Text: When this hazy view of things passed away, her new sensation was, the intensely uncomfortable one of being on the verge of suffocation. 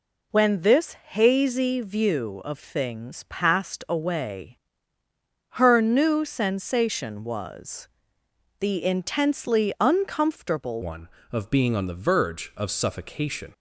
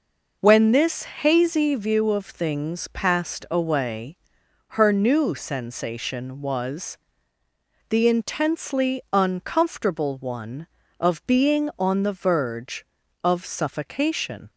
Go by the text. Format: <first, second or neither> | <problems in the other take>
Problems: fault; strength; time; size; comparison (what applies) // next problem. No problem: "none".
second | pauses between "this" and "hazy"; slight; at 0.9 s; 0.16 s long // changes voice at "one"; from 10.8 s on; 2.7 s long